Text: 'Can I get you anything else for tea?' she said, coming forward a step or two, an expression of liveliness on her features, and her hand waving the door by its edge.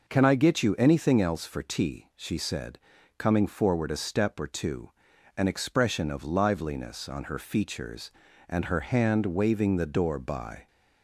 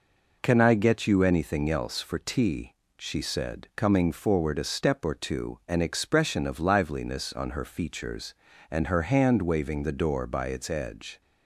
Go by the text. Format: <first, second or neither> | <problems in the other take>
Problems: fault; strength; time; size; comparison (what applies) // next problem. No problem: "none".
second | stops before "its edge"; at 10.6 s